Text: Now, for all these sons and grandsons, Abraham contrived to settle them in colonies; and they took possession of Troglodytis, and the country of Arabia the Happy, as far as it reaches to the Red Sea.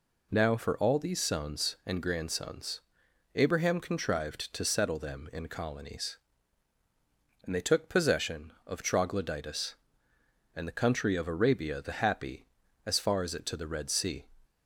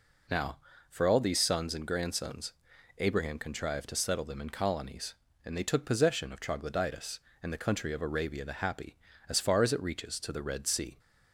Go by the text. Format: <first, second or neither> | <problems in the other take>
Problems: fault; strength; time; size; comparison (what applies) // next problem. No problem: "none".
second | skips "reaches"; at 13.4 s